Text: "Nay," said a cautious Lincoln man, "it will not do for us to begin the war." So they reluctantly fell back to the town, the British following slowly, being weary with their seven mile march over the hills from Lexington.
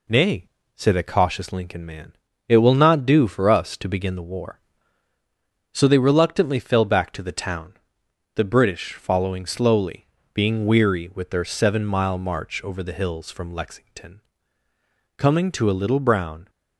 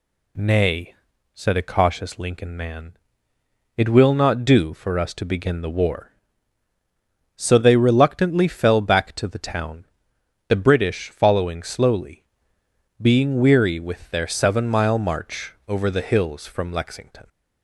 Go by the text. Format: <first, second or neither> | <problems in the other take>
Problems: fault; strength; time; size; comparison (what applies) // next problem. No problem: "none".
second | goes on to say "Coming to a little brown"; from 15.1 s on; 1.3 s long